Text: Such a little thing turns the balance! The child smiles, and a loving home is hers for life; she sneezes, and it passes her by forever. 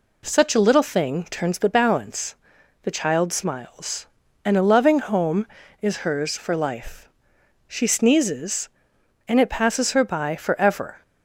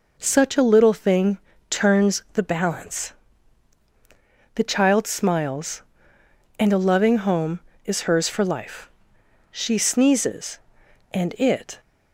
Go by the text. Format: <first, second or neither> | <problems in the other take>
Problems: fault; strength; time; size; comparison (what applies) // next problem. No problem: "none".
first | pauses between "thing" and "turns"; slight; at 1.3 s; 0.32 s long // stops before "passes her by forever"; at 11.7 s